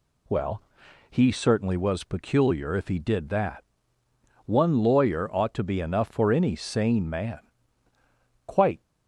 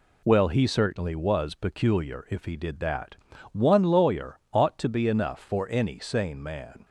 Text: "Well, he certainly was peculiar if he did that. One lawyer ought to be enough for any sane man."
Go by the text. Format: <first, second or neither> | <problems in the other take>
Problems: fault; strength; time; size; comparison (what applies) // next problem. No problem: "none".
second | goes on to say "Quite"; slight; from 8.4 s on; 0.36 s long